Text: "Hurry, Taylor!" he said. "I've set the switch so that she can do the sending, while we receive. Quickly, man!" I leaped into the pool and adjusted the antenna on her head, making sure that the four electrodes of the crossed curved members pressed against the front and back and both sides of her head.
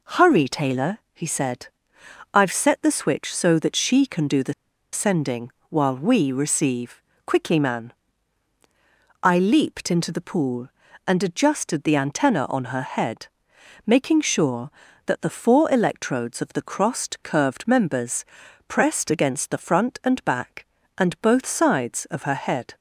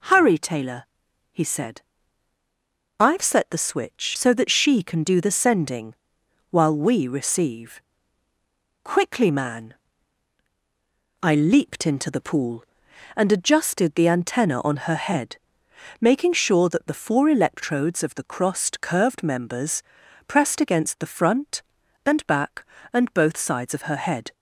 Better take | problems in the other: second | pauses between "the" and "sending"; at 4.5 s; 0.39 s long // pauses between "members" and "pressed"; at 18.2 s; 0.42 s long; also in the second

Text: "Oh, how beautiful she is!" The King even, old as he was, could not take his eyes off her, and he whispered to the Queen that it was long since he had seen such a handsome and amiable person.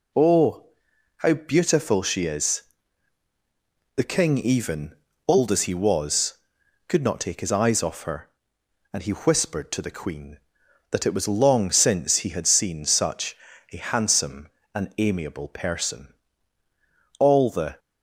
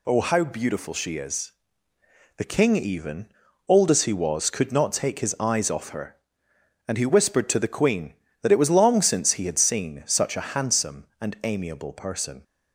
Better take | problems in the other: second | pauses between "such" and "a"; slight; at 13.3 s; 0.34 s long // goes on to say "All the"; from 17.1 s on; 0.60 s long

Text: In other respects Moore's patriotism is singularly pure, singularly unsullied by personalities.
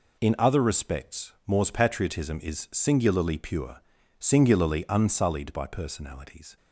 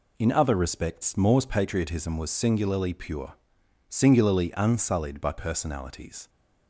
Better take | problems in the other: first | says "was" for "is"; at 2.1 s

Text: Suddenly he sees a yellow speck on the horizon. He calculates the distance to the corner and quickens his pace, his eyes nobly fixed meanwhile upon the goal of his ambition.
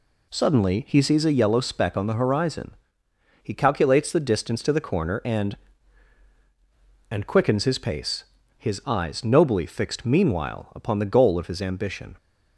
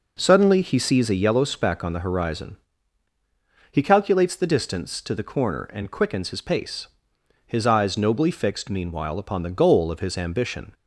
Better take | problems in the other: second | says "and" twice; at 7.0 s

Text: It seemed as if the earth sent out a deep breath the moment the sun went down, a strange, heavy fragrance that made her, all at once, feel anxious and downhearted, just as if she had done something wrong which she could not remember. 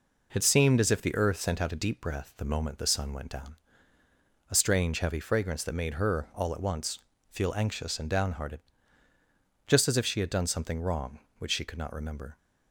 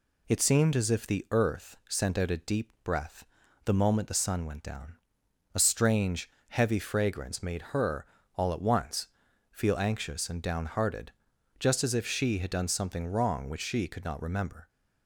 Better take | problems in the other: first | pauses between "breath" and "the"; at 3.2 s; 0.40 s long // skips "that"; at 7.4 s

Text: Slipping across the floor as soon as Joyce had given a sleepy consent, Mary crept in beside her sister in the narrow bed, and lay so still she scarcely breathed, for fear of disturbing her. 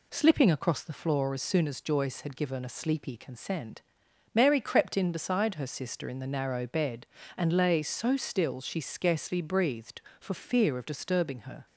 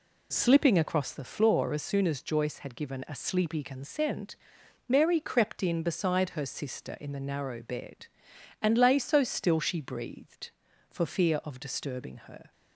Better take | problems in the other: first | skips "scarcely"; at 9.8 s

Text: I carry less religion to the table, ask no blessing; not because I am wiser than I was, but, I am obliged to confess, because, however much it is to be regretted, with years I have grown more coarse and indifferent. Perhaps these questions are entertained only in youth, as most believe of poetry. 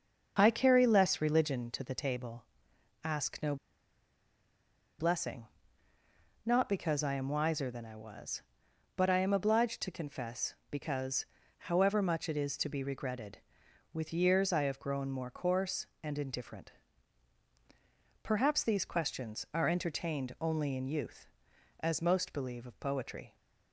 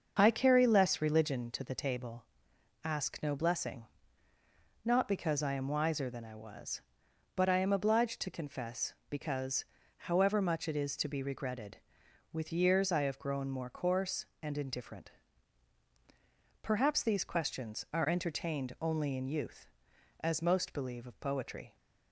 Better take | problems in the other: second | starts louder than the rest; until 1.4 s; 6.5 dB; also in the second // pauses between "no" and "blessing"; strong; at 3.5 s; 1.4 s long

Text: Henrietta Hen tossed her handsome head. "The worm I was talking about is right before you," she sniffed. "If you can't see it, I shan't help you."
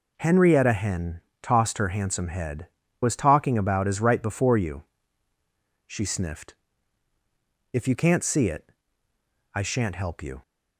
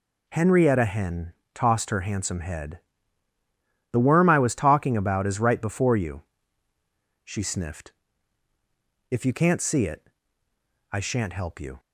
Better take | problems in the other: second | pauses between "Hen" and "tossed"; slight; at 1.2 s; 0.22 s long; slight in the second // skips "The worm I"; at 2.8 s

